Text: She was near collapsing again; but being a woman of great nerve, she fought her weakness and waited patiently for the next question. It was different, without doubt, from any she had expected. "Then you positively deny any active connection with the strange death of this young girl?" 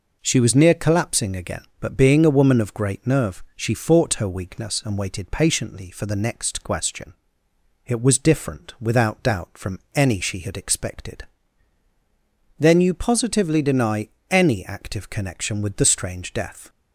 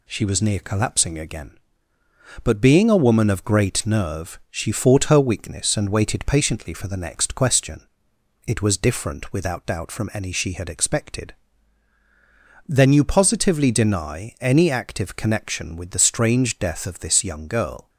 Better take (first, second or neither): second